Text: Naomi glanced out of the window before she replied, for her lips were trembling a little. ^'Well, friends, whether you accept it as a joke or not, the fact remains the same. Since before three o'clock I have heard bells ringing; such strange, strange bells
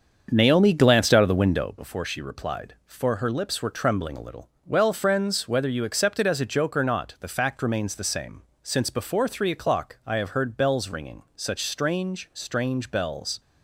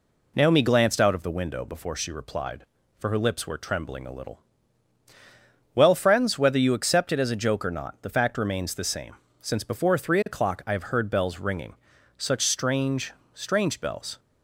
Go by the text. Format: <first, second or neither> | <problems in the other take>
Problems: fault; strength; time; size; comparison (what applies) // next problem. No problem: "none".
second | starts louder than the rest; until 1.8 s; 7 dB